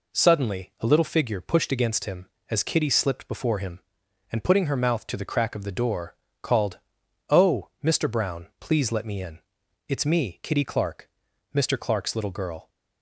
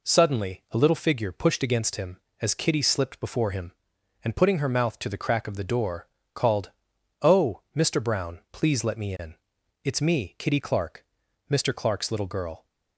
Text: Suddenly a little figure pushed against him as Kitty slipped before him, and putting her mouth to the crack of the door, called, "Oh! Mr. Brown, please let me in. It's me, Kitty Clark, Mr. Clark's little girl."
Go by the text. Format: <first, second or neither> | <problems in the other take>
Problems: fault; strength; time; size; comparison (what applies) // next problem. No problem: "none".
neither | none